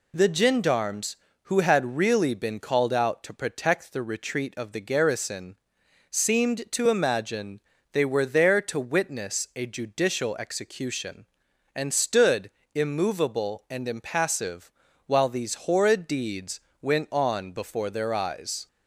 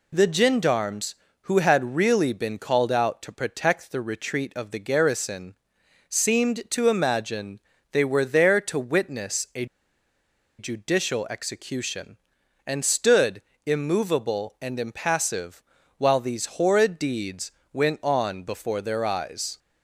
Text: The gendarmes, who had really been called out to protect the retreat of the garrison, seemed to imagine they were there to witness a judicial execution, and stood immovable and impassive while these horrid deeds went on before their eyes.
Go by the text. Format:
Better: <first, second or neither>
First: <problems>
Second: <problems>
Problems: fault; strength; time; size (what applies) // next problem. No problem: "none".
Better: first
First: pauses between "imagine" and "they"; slight; at 7.5 s; 0.32 s long // pauses between "stood" and "immovable"; slight; at 12.5 s; 0.24 s long // pauses between "impassive" and "while"; at 14.6 s; 0.38 s long // pauses between "deeds" and "went"; slight; at 16.5 s; 0.20 s long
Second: pauses between "imagine" and "they"; slight; at 7.5 s; 0.32 s long // pauses between "a" and "judicial"; noticeable; at 9.6 s; 0.93 s long // pauses between "stood" and "immovable"; slight; at 13.4 s; 0.24 s long // pauses between "impassive" and "while"; at 15.6 s; 0.38 s long // pauses between "deeds" and "went"; slight; at 17.5 s; 0.20 s long